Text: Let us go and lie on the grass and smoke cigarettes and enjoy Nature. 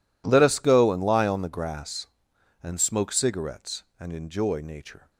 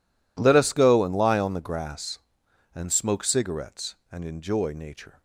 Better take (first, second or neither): neither